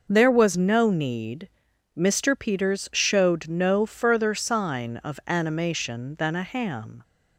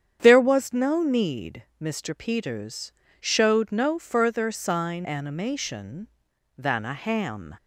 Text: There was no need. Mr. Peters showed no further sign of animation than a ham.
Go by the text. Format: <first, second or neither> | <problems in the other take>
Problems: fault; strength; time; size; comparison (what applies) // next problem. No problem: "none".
first | starts louder than the rest; strong; until 1.2 s; 8.5 dB // pauses between "Peters" and "showed"; slight; at 2.9 s; 0.28 s long // skips "of"; at 5.0 s